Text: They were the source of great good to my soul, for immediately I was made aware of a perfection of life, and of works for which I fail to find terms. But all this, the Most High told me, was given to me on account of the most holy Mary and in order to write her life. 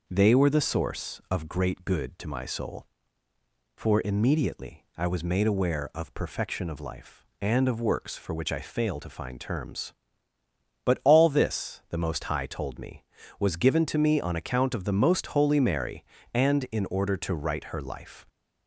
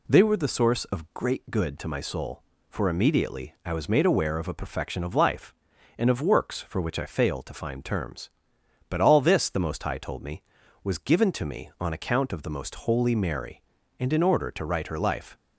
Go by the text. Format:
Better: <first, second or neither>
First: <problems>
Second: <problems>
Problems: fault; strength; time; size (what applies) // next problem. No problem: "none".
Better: second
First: skips "a"; at 6.1 s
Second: none